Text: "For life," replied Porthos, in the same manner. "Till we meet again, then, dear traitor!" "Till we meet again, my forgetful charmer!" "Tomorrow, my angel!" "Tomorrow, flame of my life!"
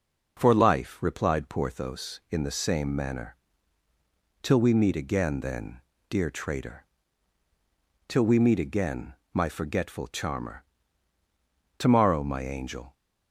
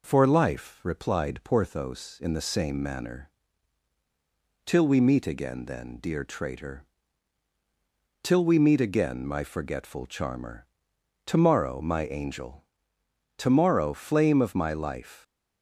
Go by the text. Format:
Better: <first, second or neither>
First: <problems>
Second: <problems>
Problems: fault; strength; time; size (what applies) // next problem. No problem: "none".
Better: second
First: stops before "Tomorrow flame of my life"; at 12.9 s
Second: none